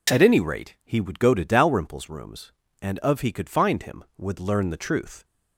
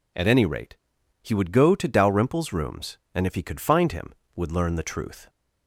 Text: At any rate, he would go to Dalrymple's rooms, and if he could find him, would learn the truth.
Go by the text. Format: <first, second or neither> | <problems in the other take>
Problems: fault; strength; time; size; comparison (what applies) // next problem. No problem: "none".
second | says "of" for "if"; at 3.0 s